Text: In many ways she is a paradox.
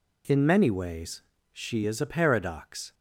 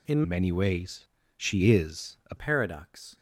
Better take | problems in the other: first | changes voice from "many" to "a"; from 0.2 to 2.3 s; 2.1 s long // pauses between "ways" and "she"; slight; at 1.0 s; 0.32 s long; slight in the first

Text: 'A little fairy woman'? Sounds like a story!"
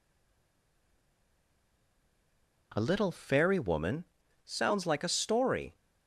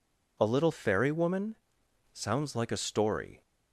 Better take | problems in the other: second | stays silent before the first word; strong; until 2.7 s; 2.7 s long

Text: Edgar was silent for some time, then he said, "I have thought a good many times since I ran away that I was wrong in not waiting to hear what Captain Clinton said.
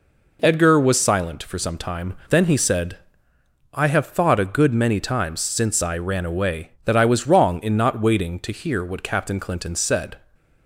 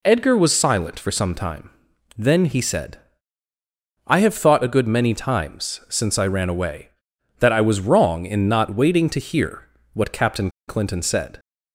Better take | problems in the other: first | pauses between "hear" and "what"; slight; at 9.6 s; 0.24 s long // pauses between "Captain" and "Clinton"; slight; at 10.5 s; 0.17 s long

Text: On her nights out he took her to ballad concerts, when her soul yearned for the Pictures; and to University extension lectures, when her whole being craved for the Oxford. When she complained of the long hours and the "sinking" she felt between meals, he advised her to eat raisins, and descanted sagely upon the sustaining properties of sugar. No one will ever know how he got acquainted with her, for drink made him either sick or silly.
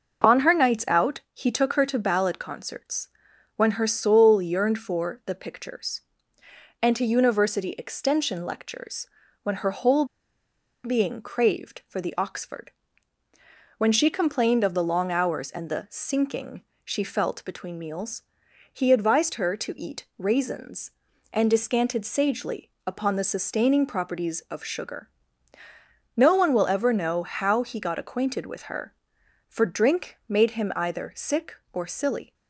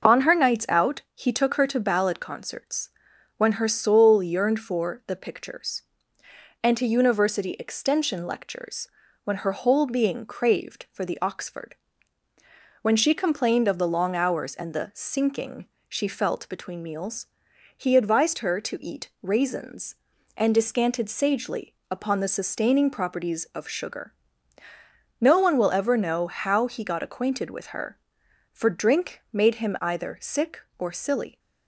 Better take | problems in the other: second | starts louder than the rest; noticeable; until 1.3 s; 6 dB; noticeable in the second // pauses between "whole" and "being"; noticeable; at 10.0 s; 0.79 s long // pauses between "sinking" and "she"; slight; at 16.6 s; 0.20 s long; slight in the second

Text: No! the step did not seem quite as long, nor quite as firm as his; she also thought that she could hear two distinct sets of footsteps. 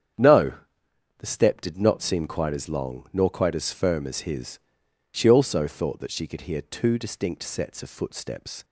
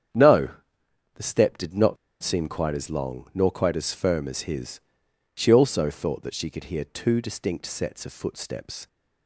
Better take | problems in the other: first | starts louder than the rest; strong; until 1.8 s; 8.5 dB; strong in the first // pauses between "not" and "seem"; slight; at 1.9 s; 0.27 s long

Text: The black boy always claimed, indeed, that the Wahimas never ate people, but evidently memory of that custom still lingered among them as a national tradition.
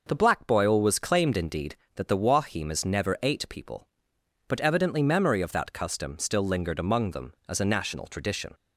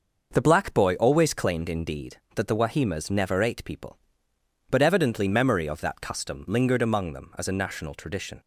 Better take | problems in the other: first | starts louder than the rest; noticeable; until 1.3 s; 6 dB // skips "still"; at 6.4 s

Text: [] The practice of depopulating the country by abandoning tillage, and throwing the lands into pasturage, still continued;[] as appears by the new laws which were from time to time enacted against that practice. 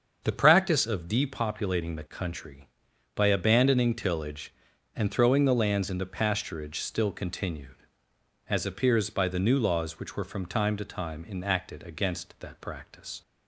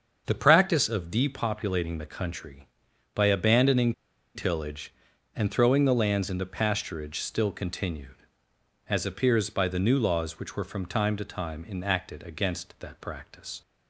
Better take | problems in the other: first | starts louder than the rest; until 1.2 s; 7 dB; also in the first // pauses between "abandoning" and "tillage"; at 3.9 s; 0.42 s long

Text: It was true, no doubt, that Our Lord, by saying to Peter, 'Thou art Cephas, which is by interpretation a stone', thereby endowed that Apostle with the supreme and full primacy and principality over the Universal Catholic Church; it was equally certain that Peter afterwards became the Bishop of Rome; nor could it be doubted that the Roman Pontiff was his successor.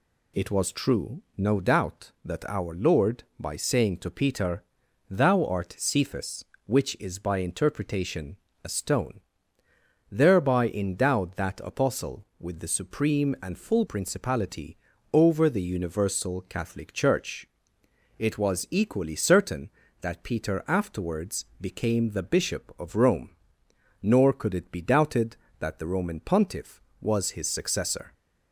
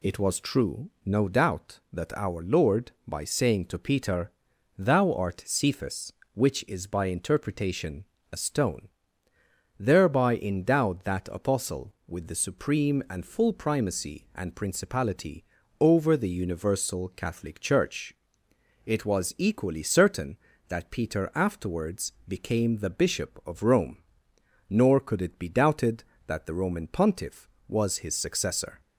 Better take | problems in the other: second | pauses between "interpretation" and "a"; slight; at 8.3 s; 0.28 s long; slight in the second // skips "primacy and"; at 13.8 s // pauses between "principality" and "over"; slight; at 14.7 s; 0.36 s long; slight in the second // pauses between "afterwards" and "became"; slight; at 21.4 s; 0.16 s long; slight in the second

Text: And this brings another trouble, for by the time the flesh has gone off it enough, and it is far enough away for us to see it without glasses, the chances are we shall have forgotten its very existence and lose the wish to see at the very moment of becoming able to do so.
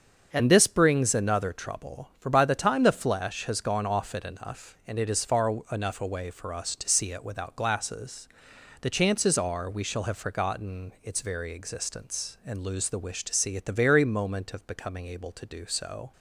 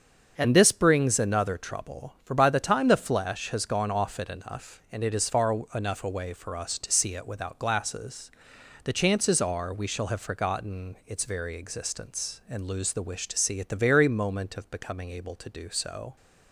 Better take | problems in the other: neither | starts louder than the rest; the same in both // pauses between "far" and "enough"; slight; the same in both

